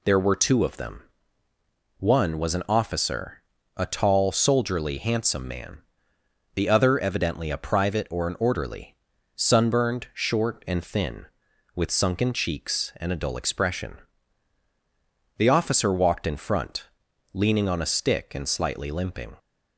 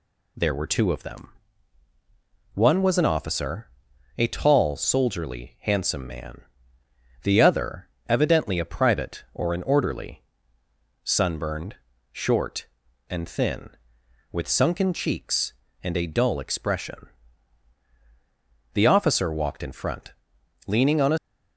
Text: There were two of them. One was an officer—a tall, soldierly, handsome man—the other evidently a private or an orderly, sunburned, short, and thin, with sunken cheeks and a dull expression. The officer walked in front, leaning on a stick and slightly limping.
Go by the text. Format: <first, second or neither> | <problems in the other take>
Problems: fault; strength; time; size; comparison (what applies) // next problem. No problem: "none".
first | pauses between "other" and "evidently"; slight; at 7.8 s; 0.22 s long // stops before "stick and slightly limping"; at 21.1 s